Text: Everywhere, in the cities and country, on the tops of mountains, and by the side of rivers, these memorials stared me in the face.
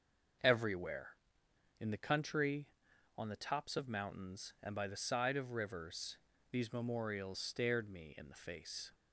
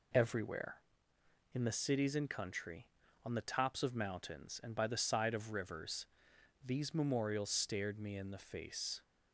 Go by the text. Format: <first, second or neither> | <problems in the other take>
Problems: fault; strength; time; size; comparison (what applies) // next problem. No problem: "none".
second | skips "cities and"; at 1.9 s